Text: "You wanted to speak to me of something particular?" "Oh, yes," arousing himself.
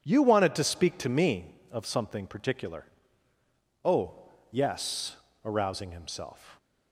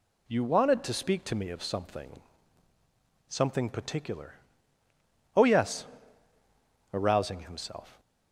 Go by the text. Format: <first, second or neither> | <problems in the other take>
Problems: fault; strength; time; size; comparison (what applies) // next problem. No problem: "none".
first | says "something" twice; at 3.2 s